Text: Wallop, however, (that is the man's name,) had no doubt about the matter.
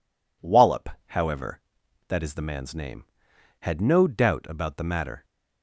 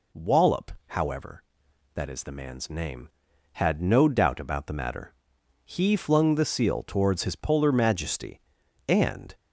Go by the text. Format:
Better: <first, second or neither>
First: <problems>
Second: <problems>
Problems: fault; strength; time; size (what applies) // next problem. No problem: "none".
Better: first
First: none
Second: goes on to say "He flung the seal towards his Polar Majesty and"; strong; from 5.6 s on; 3.7 s long